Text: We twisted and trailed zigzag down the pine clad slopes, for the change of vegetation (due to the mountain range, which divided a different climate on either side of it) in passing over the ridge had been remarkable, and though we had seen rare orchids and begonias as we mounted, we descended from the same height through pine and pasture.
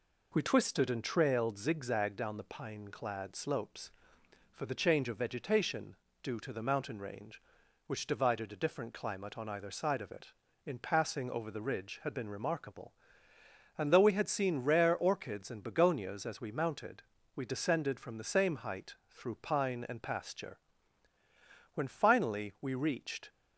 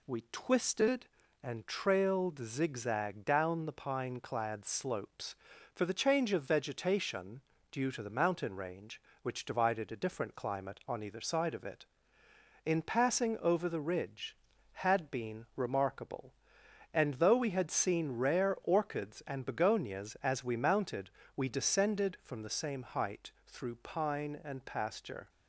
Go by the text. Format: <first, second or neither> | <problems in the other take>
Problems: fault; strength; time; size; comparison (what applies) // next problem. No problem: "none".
second | pauses between "height" and "through"; slight; at 18.9 s; 0.16 s long // goes on to say "When finally we reached"; from 21.7 s on; 1.5 s long